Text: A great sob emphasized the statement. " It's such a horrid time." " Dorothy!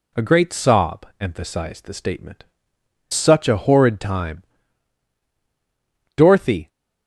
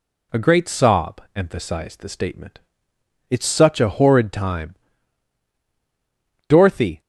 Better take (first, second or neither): second